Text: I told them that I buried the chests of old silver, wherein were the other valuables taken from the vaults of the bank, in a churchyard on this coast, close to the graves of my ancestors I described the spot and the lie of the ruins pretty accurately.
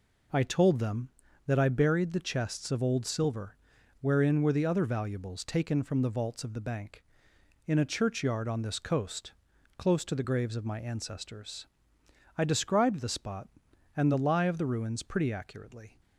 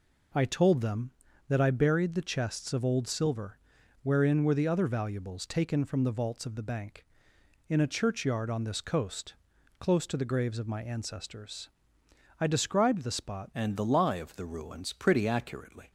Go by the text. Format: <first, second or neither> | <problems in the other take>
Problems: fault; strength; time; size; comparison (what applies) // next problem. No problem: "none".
first | pauses between "ancestors" and "I"; noticeable; at 11.6 s; 0.70 s long; noticeable in the first // changes voice at "and"; from 13.5 s on; 2.4 s long